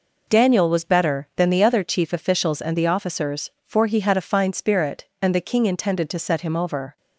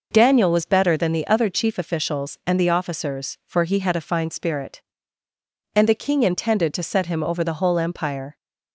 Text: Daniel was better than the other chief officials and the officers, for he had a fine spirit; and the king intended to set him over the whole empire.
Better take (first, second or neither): second